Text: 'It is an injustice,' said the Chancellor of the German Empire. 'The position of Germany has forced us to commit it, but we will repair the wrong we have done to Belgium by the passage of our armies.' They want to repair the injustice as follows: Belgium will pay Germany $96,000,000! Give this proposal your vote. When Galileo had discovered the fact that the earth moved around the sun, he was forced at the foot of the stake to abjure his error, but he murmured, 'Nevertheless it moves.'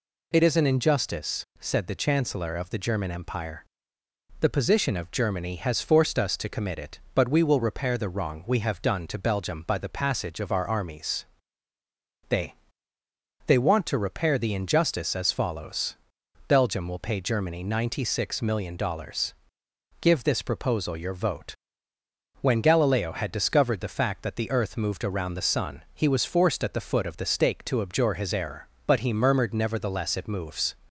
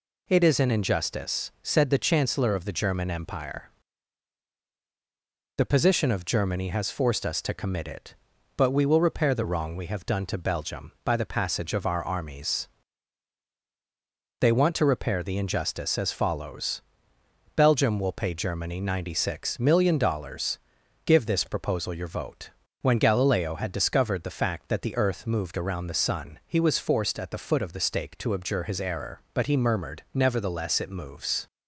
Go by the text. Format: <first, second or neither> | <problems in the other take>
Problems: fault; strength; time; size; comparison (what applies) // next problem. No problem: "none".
second | says "They" twice; at 13.4 s